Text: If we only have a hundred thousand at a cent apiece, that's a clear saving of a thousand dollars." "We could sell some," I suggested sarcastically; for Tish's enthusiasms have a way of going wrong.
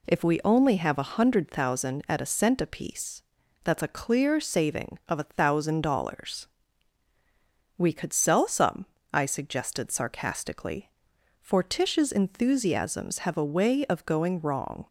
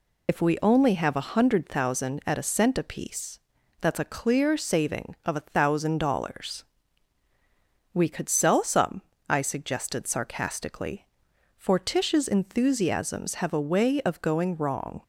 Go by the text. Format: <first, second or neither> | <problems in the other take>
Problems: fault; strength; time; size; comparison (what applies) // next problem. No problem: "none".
first | loses the start of "If"; at 0.2 s; 90 ms